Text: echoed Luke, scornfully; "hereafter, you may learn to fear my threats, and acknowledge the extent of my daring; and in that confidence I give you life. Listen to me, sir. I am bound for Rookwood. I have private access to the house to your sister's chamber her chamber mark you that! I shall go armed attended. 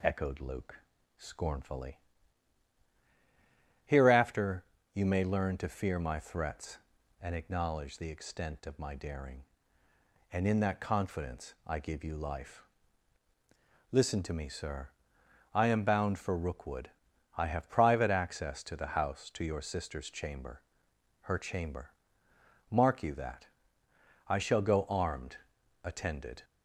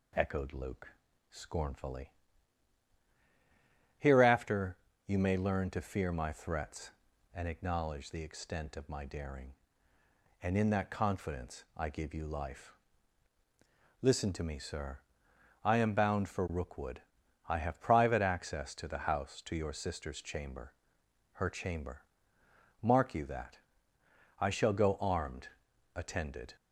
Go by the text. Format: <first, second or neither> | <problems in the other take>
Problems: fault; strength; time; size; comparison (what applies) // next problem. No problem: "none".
neither | pauses between "chamber" and "her"; noticeable; the same in both // pauses between "chamber" and "mark"; noticeable; the same in both // pauses between "armed" and "attended"; the same in both